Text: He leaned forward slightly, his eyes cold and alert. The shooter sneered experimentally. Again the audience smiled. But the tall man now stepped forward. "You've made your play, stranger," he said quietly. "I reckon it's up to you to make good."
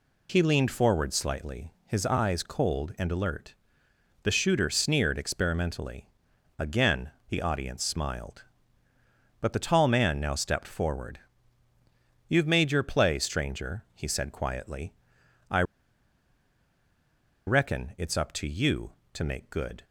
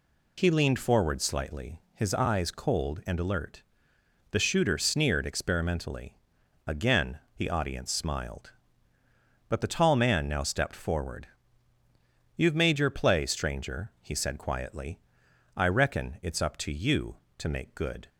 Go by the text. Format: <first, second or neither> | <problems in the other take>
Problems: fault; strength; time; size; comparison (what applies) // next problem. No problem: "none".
second | pauses between "Again" and "the"; slight; at 7.1 s; 0.20 s long; slight in the second // pauses between "I" and "reckon"; strong; at 15.6 s; 1.8 s long